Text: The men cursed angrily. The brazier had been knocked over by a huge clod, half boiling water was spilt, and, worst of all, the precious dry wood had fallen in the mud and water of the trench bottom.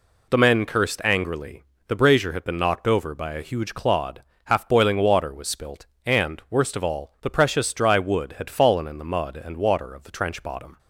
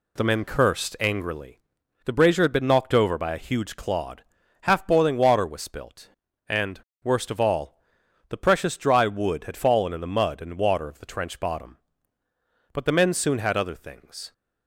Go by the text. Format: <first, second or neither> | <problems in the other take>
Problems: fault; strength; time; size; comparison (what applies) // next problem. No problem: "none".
first | goes on to say "But the men soon had other things"; from 12.7 s on; 1.6 s long